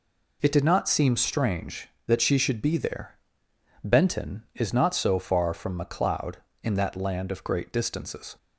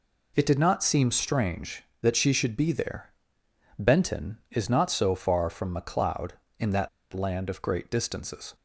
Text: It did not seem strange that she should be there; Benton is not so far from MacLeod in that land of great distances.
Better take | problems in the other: first | pauses between "that" and "land"; slight; at 6.8 s; 0.23 s long

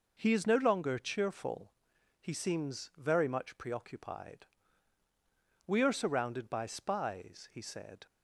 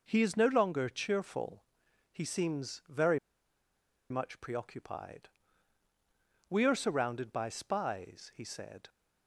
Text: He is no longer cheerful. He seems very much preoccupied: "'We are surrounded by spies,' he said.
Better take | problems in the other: first | pauses between "very" and "much"; noticeable; at 3.1 s; 0.91 s long

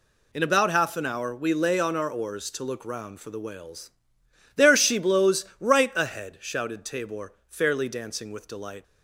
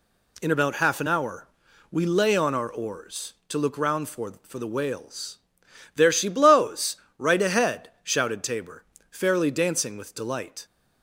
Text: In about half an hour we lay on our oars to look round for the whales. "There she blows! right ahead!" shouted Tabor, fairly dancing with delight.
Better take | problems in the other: first | pauses between "hour" and "we"; at 1.4 s; 0.44 s long // says "for" twice; at 4.4 s

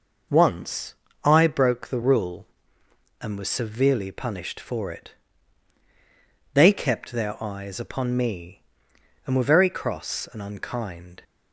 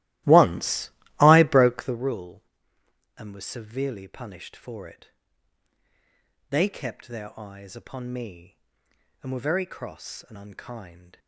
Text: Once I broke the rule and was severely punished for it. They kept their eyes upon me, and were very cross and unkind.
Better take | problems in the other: first | starts louder than the rest; strong; until 2.0 s; 16 dB // pauses between "Once" and "I"; slight; at 0.8 s; 0.30 s long; slight in the first

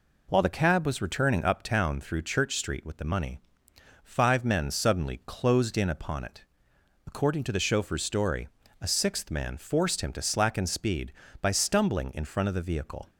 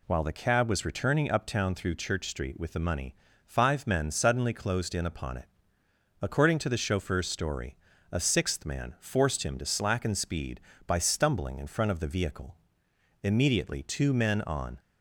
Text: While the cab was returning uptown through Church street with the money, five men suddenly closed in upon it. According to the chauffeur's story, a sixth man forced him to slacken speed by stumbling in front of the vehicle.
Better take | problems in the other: first | goes on to say "Immediately two men on"; from 13.1 s on; 1.6 s long

